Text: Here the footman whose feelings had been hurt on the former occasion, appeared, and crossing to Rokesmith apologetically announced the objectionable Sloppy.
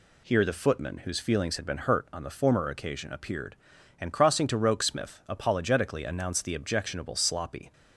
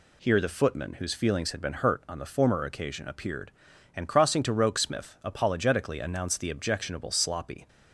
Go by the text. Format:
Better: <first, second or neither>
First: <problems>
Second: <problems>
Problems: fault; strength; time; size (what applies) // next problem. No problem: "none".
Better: neither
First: none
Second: none